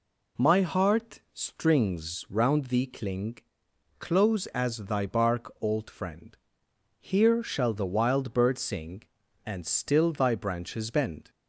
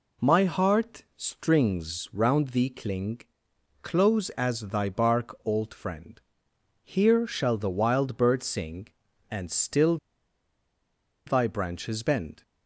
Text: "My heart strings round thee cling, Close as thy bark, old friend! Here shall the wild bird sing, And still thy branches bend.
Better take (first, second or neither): first